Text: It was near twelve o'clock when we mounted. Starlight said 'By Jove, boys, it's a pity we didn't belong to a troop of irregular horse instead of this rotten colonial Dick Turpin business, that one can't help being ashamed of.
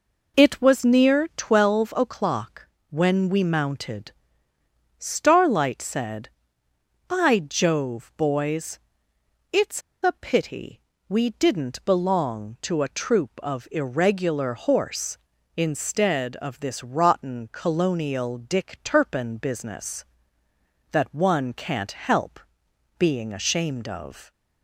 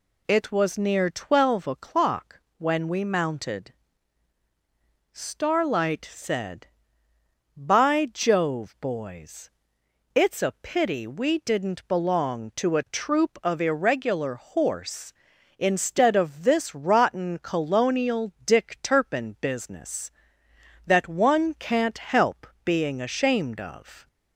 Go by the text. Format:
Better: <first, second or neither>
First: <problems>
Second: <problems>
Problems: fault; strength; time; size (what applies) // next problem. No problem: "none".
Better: second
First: pauses between "o'clock" and "when"; slight; at 2.6 s; 0.22 s long // pauses between "it's" and "a"; slight; at 9.8 s; 0.22 s long // pauses between "pity" and "we"; slight; at 10.8 s; 0.26 s long // pauses between "help" and "being"; noticeable; at 22.3 s; 0.58 s long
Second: pauses between "o'clock" and "when"; slight; at 2.3 s; 0.18 s long // pauses between "help" and "being"; slight; at 22.4 s; 0.20 s long